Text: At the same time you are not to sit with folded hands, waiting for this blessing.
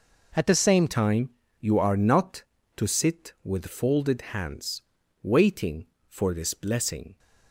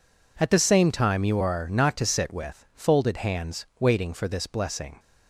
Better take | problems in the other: second | changes voice at "time"; from 0.8 s on; 6.3 s long // pauses between "time" and "you"; slight; at 1.3 s; 0.30 s long

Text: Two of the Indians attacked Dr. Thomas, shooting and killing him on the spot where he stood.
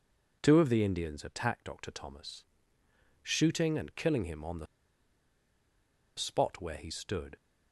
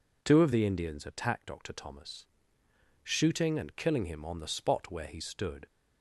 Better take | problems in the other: second | pauses between "the" and "spot"; strong; at 4.6 s; 1.5 s long

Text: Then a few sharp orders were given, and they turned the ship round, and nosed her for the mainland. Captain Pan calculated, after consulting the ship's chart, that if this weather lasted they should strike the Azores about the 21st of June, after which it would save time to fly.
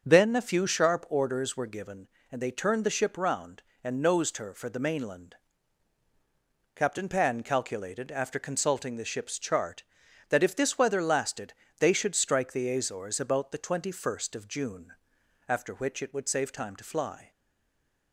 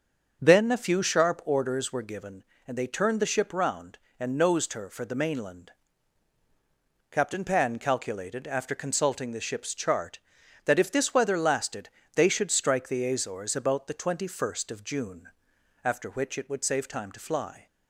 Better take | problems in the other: second | starts louder than the rest; until 1.0 s; 6.5 dB; also in the second // pauses between "lasted" and "they"; slight; at 11.5 s; 0.26 s long; slight in the second // stays silent after the last word; slight; from 17.3 s on; 0.8 s long

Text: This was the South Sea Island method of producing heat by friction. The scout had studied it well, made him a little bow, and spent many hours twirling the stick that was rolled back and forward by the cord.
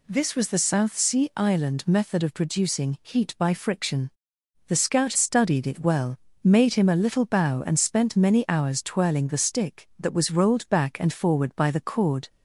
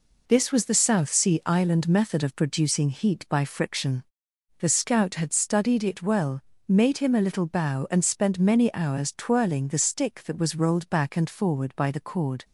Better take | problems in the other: second | skips "had"; at 5.1 s

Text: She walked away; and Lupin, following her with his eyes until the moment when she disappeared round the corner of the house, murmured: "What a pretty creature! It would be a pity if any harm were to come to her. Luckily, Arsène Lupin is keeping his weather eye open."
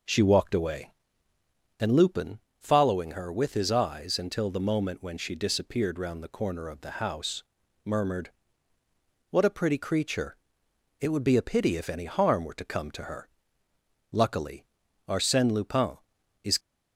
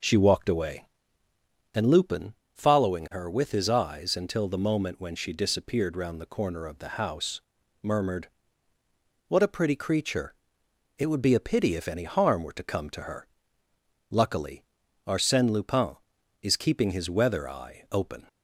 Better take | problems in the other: second | stops before "keeping his weather eye open"; at 16.5 s

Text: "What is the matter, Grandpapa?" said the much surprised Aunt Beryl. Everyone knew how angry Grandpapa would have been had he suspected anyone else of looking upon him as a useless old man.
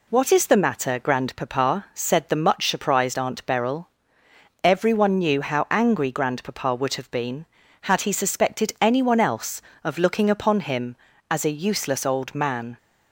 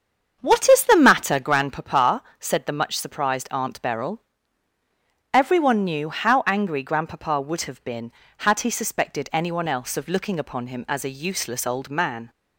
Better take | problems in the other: first | starts louder than the rest; strong; until 1.5 s; 7.5 dB

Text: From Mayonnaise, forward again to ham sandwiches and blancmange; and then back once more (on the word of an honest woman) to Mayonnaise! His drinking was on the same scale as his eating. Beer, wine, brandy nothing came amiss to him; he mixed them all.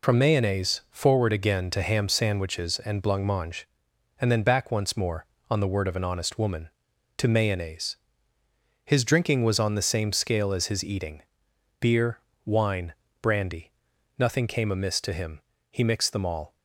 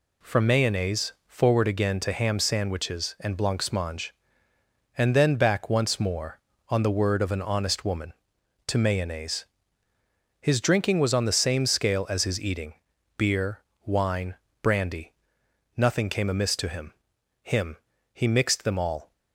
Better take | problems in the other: first | pauses between "brandy" and "nothing"; noticeable; at 15.1 s; 0.64 s long; noticeable in the first // says "him" twice; at 17.4 s

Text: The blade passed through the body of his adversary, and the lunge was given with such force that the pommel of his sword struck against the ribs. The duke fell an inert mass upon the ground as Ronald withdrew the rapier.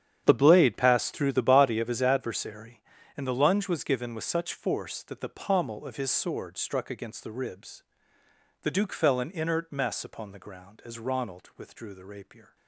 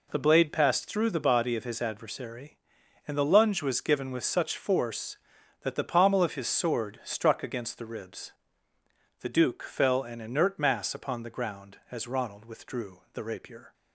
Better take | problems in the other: second | starts louder than the rest; strong; until 1.2 s; 9 dB // says "mess" for "mass"; at 9.7 s

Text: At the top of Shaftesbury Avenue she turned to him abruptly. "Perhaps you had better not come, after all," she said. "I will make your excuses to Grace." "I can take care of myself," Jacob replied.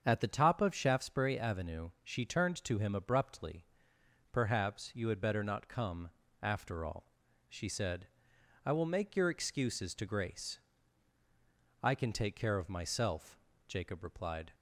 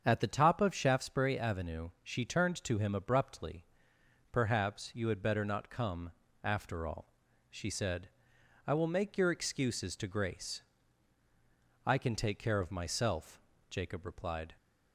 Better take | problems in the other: neither | starts louder than the rest; strong; the same in both

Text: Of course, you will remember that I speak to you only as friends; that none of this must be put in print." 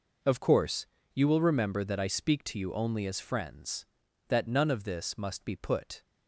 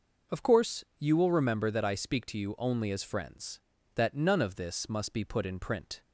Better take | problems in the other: second | stops before "in print"; at 6.0 s

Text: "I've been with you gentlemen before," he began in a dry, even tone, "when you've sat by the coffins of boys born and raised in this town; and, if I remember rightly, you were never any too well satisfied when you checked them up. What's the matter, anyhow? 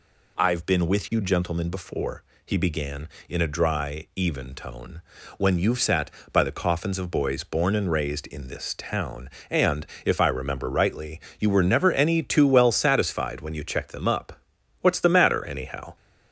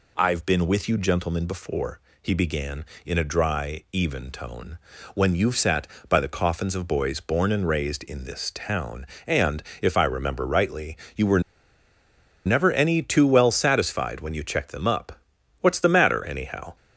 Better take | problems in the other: first | pauses between "were" and "never"; at 11.4 s; 1.0 s long

